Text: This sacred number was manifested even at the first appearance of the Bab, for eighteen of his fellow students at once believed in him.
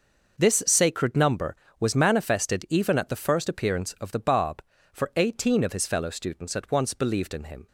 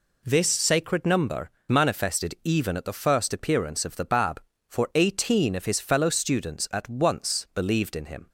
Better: first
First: none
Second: skips "was"; at 1.5 s

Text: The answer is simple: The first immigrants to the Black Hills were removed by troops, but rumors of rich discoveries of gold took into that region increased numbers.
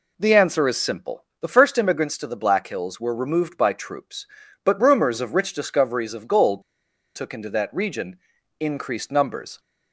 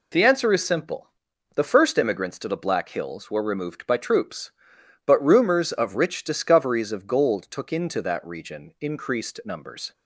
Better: second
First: pauses between "gold" and "took"; noticeable; at 6.6 s; 0.53 s long // pauses between "region" and "increased"; at 8.1 s; 0.40 s long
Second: none

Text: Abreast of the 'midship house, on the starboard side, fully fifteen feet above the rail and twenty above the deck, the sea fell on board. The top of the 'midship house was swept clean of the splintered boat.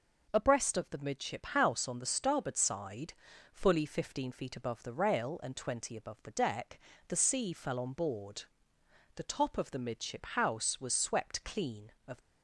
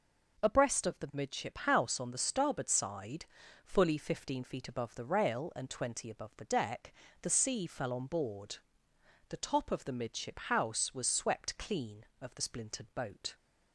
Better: second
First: stops before "the splintered boat"; at 12.1 s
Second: none

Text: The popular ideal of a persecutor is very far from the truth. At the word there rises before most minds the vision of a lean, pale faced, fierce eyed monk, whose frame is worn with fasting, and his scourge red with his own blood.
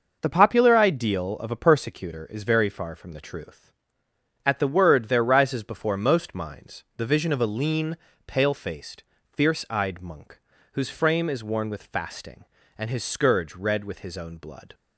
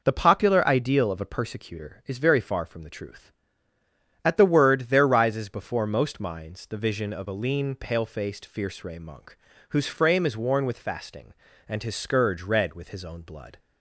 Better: first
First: none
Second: says "ray" for "eyed"; at 8.8 s

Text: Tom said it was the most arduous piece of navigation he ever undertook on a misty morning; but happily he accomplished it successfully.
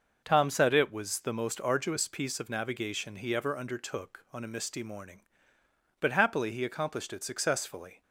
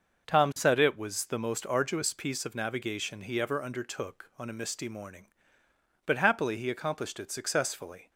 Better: neither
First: starts louder than the rest; noticeable; until 1.2 s; 6 dB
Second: starts louder than the rest; noticeable; until 1.3 s; 6 dB

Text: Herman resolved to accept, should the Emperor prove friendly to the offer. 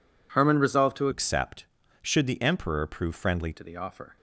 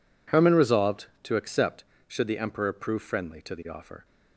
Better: second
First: changes voice from "accept" to "friendly"; from 1.1 to 3.5 s; 2.4 s long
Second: none

